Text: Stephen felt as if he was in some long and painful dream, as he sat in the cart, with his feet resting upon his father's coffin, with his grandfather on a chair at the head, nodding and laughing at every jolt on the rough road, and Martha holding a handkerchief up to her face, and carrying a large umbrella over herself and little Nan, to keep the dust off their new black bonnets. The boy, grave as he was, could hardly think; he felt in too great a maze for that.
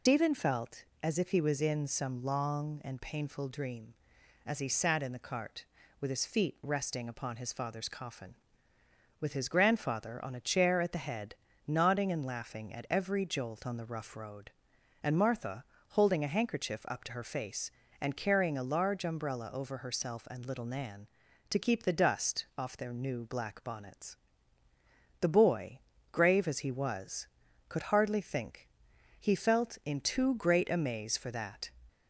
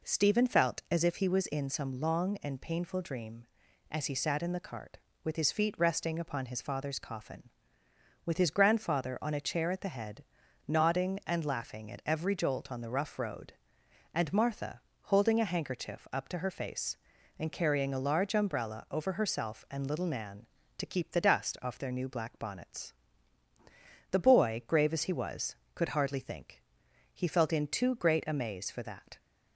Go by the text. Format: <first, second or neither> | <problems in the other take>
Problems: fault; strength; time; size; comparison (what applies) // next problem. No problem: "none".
second | loses the start of "Stephen"; at 0.0 s; 150 ms // pauses between "Martha" and "holding"; slight; at 15.6 s; 0.24 s long; slight in the second